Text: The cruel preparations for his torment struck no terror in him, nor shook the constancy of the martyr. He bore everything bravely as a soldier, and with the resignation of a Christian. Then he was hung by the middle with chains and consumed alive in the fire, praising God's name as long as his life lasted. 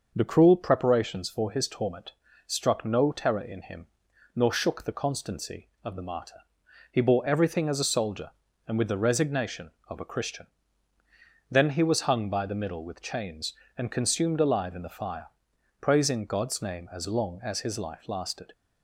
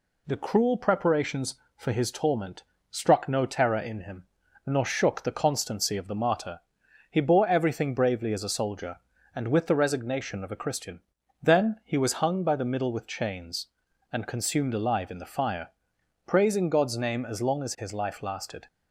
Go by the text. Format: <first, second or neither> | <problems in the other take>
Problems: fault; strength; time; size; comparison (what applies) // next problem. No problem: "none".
second | starts louder than the rest; until 1.1 s; 6 dB // pauses between "torment" and "struck"; slight; at 2.1 s; 0.32 s long; slight in the second // skips "bravely"; at 7.6 s